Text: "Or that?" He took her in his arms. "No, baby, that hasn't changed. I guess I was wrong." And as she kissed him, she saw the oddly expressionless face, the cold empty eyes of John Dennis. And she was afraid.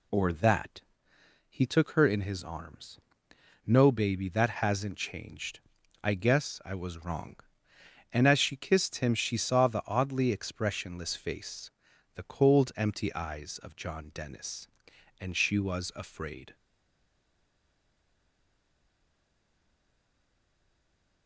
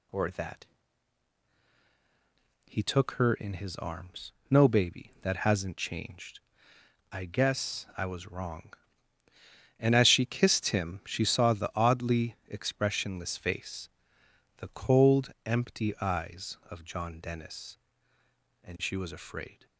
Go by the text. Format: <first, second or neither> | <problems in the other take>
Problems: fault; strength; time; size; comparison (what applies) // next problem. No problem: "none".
second | stays silent after the last word; strong; from 16.5 s on; 4.7 s long